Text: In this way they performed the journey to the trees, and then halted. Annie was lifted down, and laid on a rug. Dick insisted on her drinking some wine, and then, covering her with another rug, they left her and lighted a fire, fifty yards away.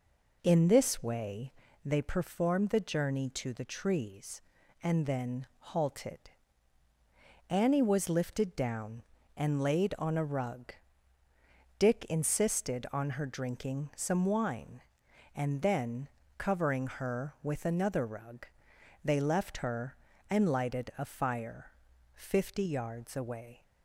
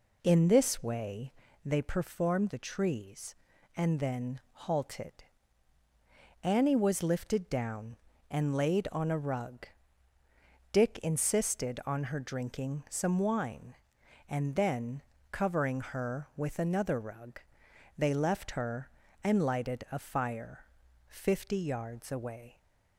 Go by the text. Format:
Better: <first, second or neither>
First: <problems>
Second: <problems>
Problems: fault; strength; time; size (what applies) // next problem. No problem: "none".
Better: first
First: pauses between "way" and "they"; slight; at 1.5 s; 0.32 s long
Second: pauses between "way" and "they"; slight; at 1.3 s; 0.32 s long // skips "the journey to"; at 2.4 s